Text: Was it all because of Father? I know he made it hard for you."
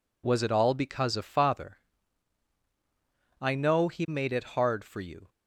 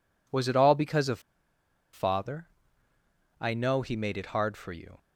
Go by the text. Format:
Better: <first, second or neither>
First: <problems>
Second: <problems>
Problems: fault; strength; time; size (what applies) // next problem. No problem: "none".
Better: first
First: none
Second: pauses between "of" and "Father"; noticeable; at 1.2 s; 0.72 s long